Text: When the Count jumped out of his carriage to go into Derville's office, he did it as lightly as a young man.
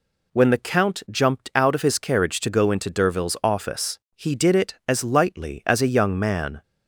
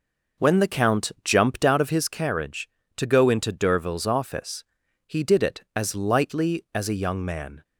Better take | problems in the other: first | starts louder than the rest; noticeable; until 2.2 s; 5.5 dB

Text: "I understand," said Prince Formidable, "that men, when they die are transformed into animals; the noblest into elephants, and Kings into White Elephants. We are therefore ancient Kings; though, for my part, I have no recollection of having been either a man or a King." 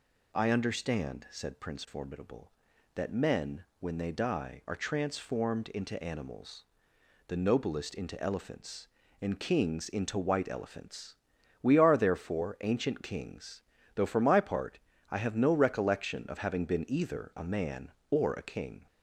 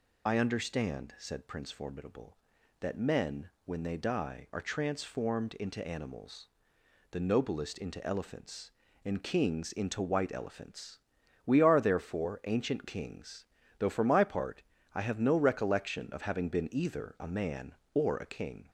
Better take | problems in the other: first | loses the start of "I"; at 0.2 s; 35 ms

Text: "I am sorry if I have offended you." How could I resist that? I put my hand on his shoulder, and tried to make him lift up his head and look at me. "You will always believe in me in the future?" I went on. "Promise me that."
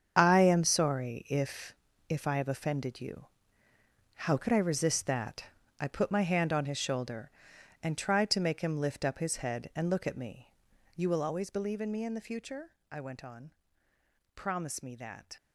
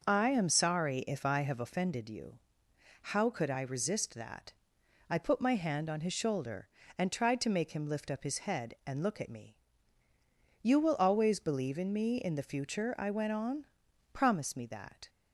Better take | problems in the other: second | starts louder than the rest; strong; until 1.1 s; 7.5 dB // says "if" twice; at 2.0 s

